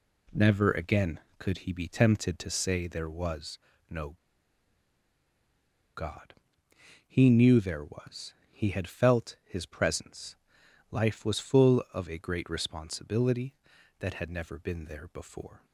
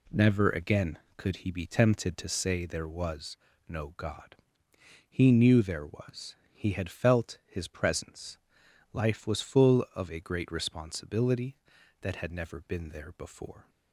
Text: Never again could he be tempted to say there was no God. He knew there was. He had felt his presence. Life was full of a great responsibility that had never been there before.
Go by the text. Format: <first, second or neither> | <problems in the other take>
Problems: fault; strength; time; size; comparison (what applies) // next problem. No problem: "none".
second | pauses between "was" and "no"; slight; at 3.5 s; 0.30 s long; slight in the second // pauses between "no" and "God"; strong; at 4.1 s; 1.8 s long